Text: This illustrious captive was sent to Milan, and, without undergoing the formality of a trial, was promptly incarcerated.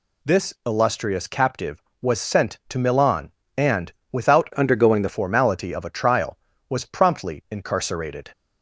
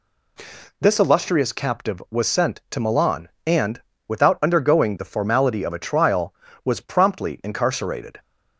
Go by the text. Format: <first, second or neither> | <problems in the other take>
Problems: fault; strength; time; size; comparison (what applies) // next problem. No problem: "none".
second | changes voice from "undergoing" to "the"; from 4.5 to 5.0 s; 0.5 s long